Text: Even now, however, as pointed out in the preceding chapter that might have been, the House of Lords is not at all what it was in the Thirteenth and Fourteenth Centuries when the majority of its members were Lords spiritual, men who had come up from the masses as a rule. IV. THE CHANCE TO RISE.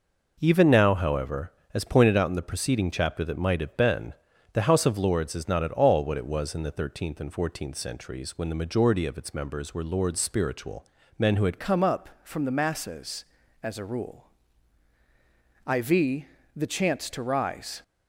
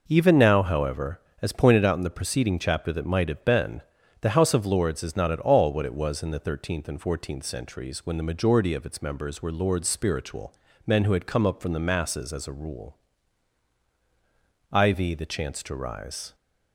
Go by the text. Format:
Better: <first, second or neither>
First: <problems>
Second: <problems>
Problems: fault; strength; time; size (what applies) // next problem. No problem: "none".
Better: second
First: changes voice at "come"; from 11.5 s on; 6.3 s long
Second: none